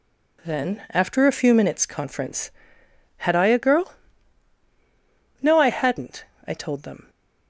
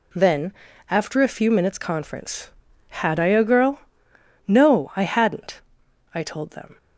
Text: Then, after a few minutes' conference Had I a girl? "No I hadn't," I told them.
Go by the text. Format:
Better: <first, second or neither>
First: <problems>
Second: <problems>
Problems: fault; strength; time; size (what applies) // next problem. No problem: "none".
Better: neither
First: none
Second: none